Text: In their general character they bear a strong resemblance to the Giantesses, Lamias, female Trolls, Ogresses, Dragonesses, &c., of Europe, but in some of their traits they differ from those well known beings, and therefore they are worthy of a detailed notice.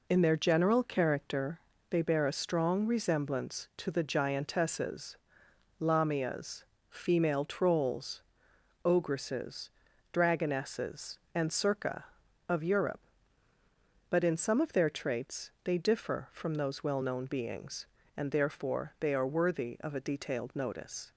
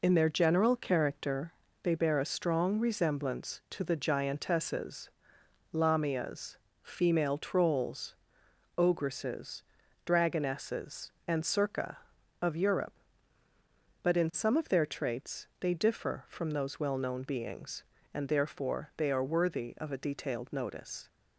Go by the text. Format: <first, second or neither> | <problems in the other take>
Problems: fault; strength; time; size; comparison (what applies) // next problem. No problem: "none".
neither | pauses between "character" and "they"; slight; the same in both